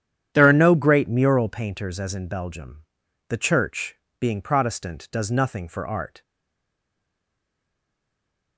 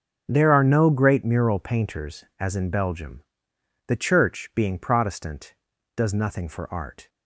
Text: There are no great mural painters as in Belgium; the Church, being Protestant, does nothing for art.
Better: second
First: starts louder than the rest; strong; until 1.3 s; 9.5 dB // stays silent after the last word; from 6.2 s on; 2.3 s long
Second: starts louder than the rest; noticeable; until 1.2 s; 6 dB

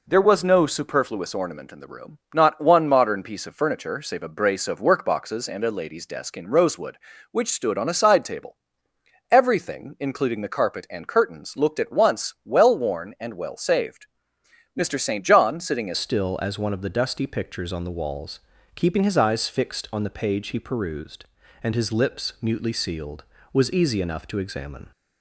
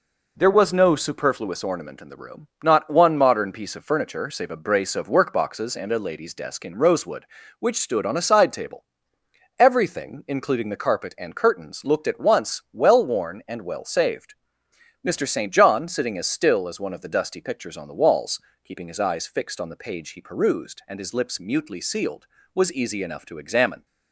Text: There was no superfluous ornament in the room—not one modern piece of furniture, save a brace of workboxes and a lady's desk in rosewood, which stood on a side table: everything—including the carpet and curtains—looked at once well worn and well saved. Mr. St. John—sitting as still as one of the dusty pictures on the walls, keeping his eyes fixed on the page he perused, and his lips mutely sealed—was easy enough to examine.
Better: second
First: changes voice at "still"; from 15.9 s on; 9.0 s long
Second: none

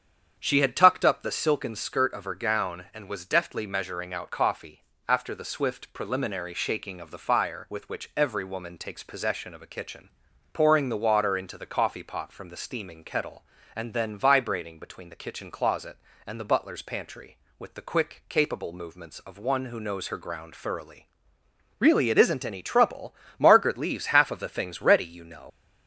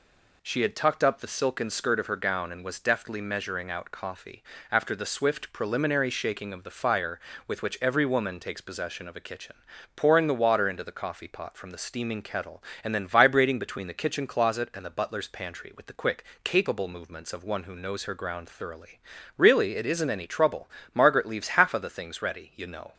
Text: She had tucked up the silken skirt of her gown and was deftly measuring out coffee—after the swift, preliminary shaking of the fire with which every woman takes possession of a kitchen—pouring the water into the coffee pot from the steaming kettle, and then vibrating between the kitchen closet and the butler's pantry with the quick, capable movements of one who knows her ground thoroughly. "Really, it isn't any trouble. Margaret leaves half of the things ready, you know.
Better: second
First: starts louder than the rest; strong; until 1.4 s; 8 dB // leaves "know" unfinished; at 25.5 s; 95 ms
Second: none

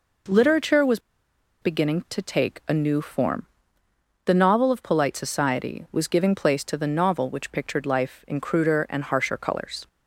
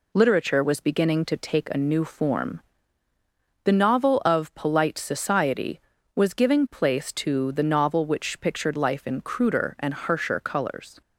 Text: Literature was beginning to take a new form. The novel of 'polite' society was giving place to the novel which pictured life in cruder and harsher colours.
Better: second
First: pauses between "was" and "beginning"; noticeable; at 0.9 s; 0.62 s long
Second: none

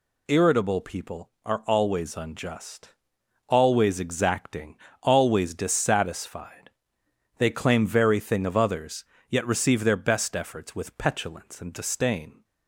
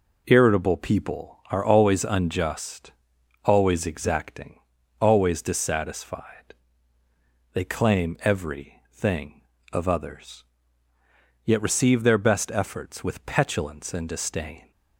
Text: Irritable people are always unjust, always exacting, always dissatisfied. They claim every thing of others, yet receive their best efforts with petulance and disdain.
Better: second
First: says "very" for "every"; at 7.8 s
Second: none

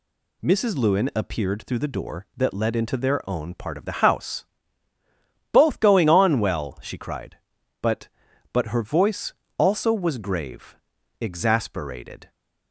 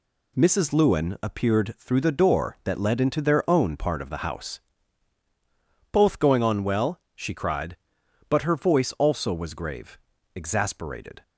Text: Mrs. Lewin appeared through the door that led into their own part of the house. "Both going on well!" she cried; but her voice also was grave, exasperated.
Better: second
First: says "but" twice; at 8.5 s // pauses between "voice" and "also"; slight; at 9.3 s; 0.24 s long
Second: none

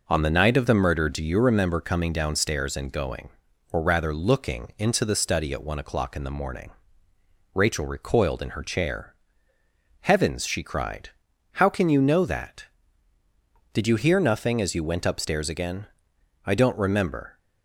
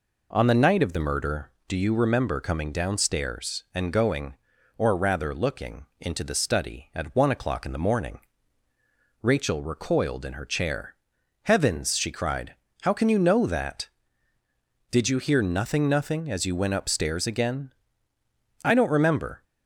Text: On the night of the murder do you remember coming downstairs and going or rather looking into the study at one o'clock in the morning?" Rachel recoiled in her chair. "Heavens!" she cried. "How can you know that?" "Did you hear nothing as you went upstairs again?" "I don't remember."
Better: first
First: none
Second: says "nothing" twice; at 15.8 s

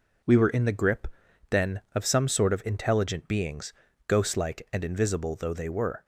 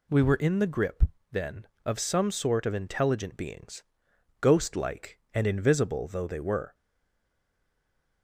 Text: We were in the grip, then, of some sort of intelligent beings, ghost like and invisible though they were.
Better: first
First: none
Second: stays silent after the last word; noticeable; from 6.7 s on; 1.5 s long

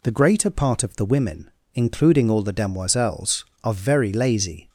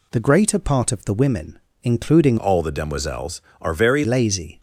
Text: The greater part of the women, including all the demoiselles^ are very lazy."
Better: first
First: none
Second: changes voice from "all" to "very"; from 2.3 to 4.0 s; 1.7 s long

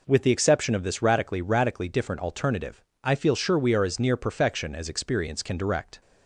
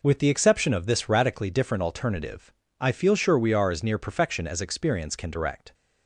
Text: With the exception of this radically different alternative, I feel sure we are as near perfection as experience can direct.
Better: second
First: says "radically" twice; at 1.4 s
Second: none

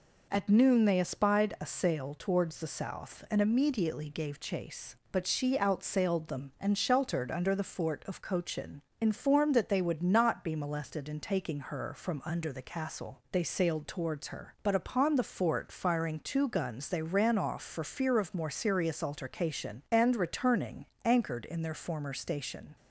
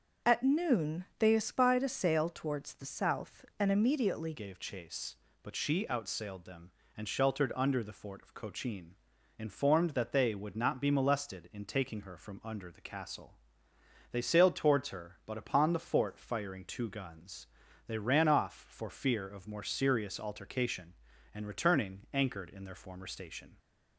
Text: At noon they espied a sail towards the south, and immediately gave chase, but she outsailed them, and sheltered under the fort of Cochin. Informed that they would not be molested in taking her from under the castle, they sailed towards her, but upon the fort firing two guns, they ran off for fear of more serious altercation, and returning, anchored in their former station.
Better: first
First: none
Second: starts louder than the rest; until 1.3 s; 6.5 dB // changes voice at "gave"; from 4.3 s on; 19.2 s long

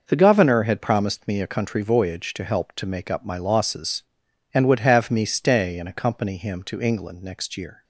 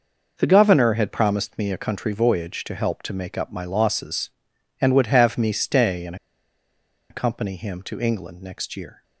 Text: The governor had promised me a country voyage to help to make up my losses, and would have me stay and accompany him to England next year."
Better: first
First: none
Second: pauses between "and" and "accompany"; noticeable; at 6.1 s; 0.95 s long

